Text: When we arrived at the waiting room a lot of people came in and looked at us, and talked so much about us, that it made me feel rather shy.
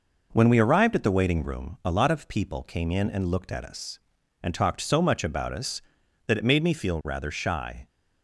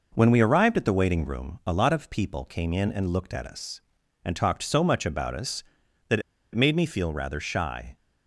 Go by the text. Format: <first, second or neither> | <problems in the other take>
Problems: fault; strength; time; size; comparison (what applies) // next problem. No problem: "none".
first | pauses between "that" and "it"; slight; at 6.1 s; 0.33 s long